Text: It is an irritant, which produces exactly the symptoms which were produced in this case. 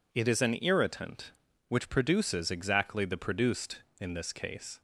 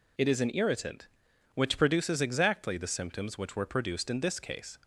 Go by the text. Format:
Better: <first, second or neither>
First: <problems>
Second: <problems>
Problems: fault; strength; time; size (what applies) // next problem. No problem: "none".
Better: second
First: skips "symptoms which were"; at 3.1 s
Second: none